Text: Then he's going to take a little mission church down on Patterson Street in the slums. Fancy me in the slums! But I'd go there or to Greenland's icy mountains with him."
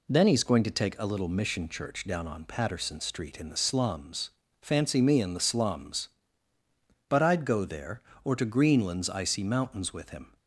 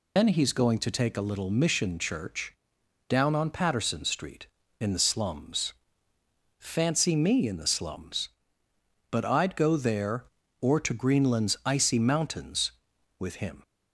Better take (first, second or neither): first